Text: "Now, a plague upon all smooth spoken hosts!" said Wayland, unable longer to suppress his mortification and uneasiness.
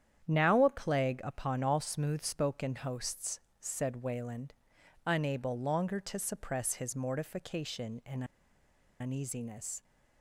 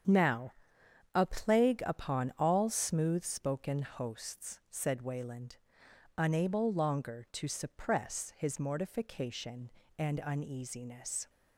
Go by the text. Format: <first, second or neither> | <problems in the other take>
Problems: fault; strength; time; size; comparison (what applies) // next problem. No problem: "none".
second | starts louder than the rest; strong; until 1.3 s; 9 dB; strong in the second // pauses between "and" and "uneasiness"; noticeable; at 8.2 s; 0.76 s long